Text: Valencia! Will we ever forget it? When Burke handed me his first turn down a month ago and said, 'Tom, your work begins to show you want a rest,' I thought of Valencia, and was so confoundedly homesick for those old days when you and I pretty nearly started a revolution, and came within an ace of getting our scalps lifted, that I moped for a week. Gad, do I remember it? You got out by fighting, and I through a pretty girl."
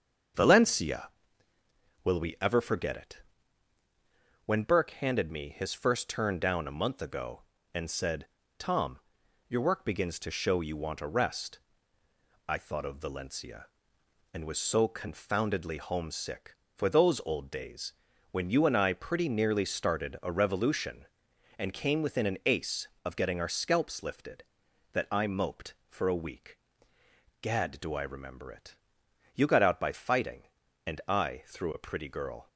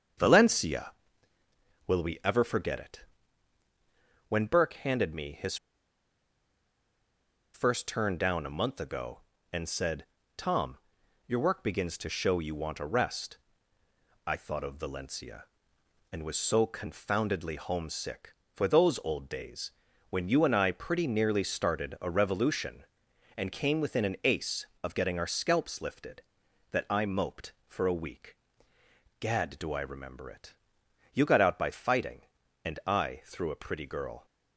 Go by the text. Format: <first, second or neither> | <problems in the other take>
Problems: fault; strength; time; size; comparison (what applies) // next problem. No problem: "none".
first | starts louder than the rest; until 2.1 s; 7 dB; also in the first // pauses between "his" and "first"; strong; at 5.5 s; 1.9 s long // pauses between "days" and "when"; at 19.7 s; 0.40 s long; also in the first